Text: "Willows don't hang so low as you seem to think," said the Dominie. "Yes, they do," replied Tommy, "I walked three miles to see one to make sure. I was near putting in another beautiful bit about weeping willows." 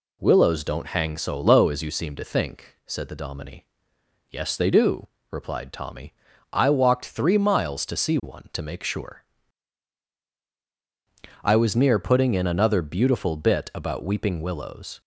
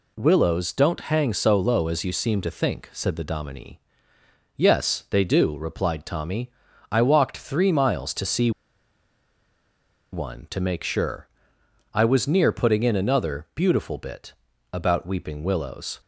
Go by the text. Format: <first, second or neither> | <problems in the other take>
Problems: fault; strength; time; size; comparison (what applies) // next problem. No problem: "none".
first | pauses between "see" and "one"; strong; at 8.5 s; 1.6 s long // pauses between "bit" and "about"; at 14.3 s; 0.40 s long